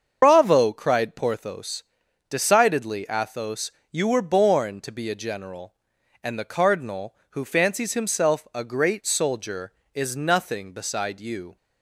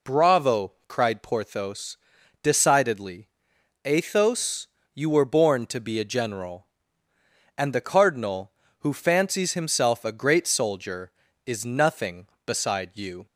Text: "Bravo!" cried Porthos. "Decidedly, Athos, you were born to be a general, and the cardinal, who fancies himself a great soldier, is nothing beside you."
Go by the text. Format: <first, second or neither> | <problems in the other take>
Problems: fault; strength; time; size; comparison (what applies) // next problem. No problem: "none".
second | loses the start of "Bravo"; at 0.2 s; 110 ms // starts louder than the rest; until 1.2 s; 7 dB